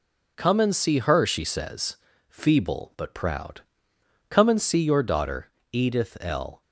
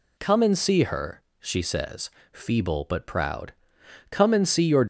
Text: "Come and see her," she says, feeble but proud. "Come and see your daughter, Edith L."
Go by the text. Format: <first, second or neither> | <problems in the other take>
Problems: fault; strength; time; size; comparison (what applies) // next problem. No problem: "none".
first | stops before "daughter Edith L"; at 4.8 s